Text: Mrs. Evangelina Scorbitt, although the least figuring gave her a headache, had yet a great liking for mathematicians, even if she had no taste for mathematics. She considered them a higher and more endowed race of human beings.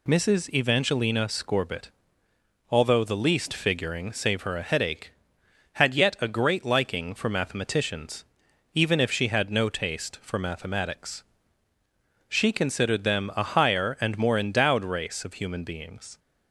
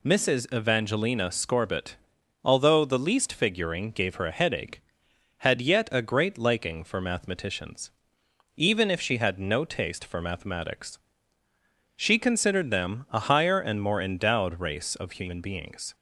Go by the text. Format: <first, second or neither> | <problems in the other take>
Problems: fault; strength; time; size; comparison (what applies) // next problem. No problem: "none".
second | says "save" for "gave"; at 4.1 s